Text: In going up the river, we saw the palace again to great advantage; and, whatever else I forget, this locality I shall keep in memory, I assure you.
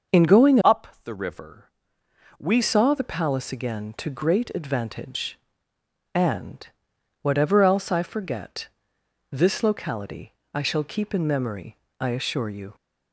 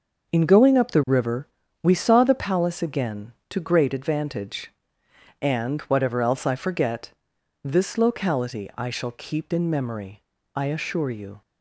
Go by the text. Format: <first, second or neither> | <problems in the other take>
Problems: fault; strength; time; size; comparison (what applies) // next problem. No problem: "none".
second | starts louder than the rest; until 1.3 s; 6.5 dB; noticeable in the second // changes voice from "up" to "we"; from 0.6 to 2.6 s; 2.0 s long // pauses between "up" and "the"; slight; at 0.8 s; 0.18 s long // pauses between "locality" and "I"; slight; at 10.3 s; 0.24 s long